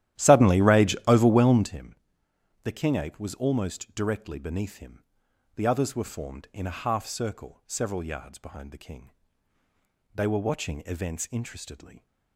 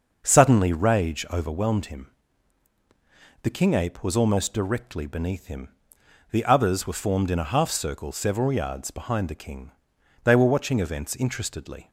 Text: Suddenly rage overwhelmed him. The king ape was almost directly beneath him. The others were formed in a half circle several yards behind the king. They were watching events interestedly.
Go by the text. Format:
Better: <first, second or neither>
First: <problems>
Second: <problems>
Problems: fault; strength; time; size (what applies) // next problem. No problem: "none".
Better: second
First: starts louder than the rest; strong; until 1.7 s; 12.5 dB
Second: none